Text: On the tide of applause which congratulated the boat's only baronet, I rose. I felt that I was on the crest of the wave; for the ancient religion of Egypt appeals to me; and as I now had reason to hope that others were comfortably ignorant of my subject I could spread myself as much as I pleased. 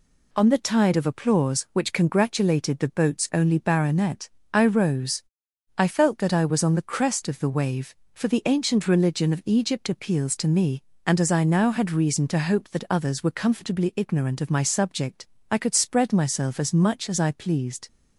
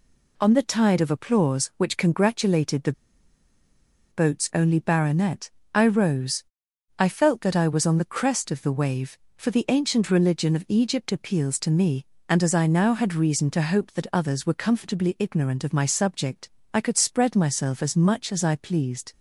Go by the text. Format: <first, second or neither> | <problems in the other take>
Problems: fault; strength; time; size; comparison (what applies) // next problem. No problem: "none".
first | pauses between "the" and "boat's"; at 2.9 s; 1.1 s long // pauses between "subject" and "I"; slight; at 16.4 s; 0.24 s long; slight in the first